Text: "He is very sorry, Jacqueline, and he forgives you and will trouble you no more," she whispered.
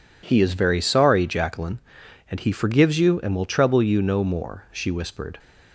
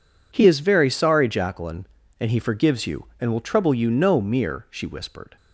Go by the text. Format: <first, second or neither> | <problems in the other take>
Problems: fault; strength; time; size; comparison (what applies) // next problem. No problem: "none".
first | says "mere" for "more"; at 4.1 s